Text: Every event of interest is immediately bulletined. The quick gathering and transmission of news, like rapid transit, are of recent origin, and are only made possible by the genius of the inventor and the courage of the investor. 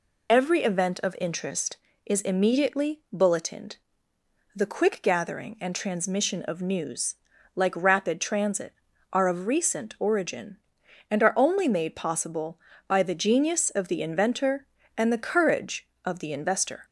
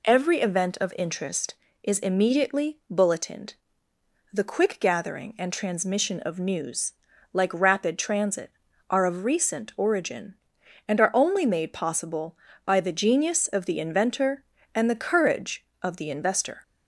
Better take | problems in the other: second | loses the start of "Every"; at 0.2 s; 30 ms

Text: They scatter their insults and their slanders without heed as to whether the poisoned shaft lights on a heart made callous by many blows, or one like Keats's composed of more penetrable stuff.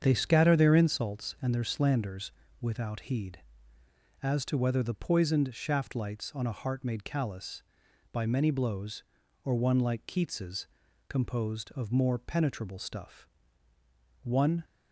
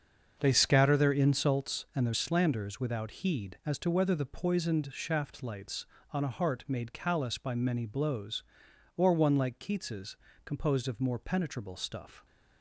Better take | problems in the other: second | starts louder than the rest; strong; until 1.0 s; 7.5 dB; also in the second // pauses between "slanders" and "without"; slight; at 2.3 s; 0.28 s long // pauses between "Keats's" and "composed"; at 10.6 s; 0.42 s long; slight in the second // goes on to say "One"; slight; from 14.2 s on; 0.40 s long

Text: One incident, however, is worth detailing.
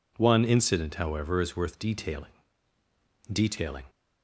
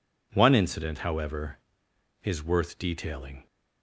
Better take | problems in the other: second | says "detailing" twice; at 3.3 s

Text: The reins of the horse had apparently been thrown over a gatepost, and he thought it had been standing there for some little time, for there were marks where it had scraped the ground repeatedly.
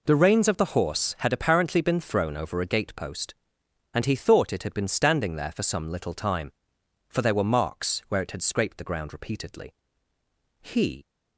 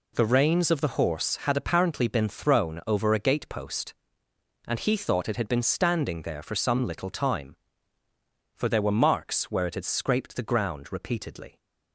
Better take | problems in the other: second | goes on to say "He"; slight; from 10.5 s on; 0.46 s long

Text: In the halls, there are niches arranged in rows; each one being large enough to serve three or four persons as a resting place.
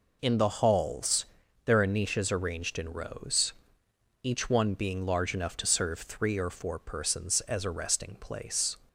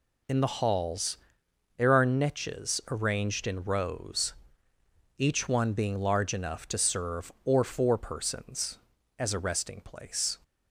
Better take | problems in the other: first | skips "three"; at 7.3 s

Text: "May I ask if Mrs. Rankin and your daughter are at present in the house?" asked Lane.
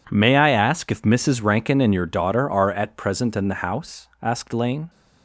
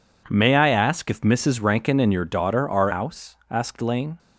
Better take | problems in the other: first | skips "at present in the"; at 2.9 s

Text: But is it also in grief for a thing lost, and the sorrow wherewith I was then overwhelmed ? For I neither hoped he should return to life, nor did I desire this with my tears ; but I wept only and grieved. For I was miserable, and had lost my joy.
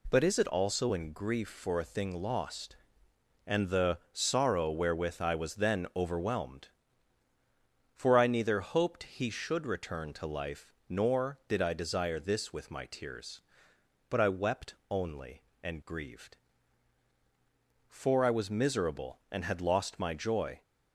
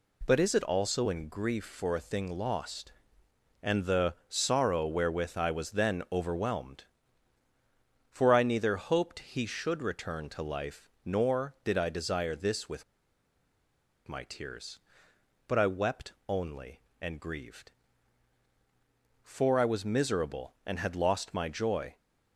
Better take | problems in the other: first | pauses between "with" and "my"; at 12.8 s; 1.2 s long // pauses between "wept" and "only"; slight; at 16.1 s; 0.16 s long; slight in the first

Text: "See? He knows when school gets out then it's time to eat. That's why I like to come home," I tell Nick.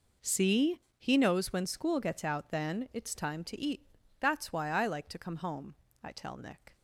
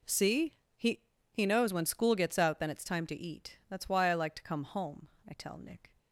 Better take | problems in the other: first | says "He" twice; at 1.3 s

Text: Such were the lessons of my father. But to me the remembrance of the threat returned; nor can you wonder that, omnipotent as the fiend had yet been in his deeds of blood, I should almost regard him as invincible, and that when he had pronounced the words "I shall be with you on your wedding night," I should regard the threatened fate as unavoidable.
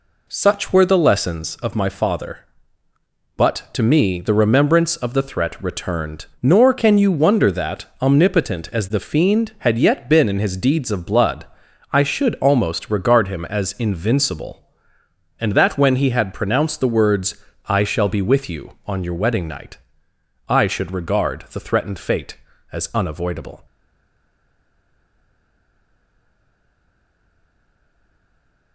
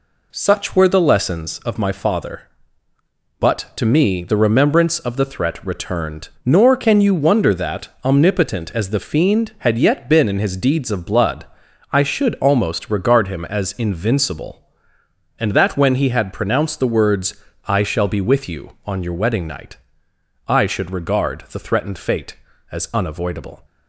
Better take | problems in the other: second | pauses between "words" and "I"; slight; at 17.3 s; 0.32 s long; slight in the second // stays silent after the last word; strong; from 23.6 s on; 5.1 s long

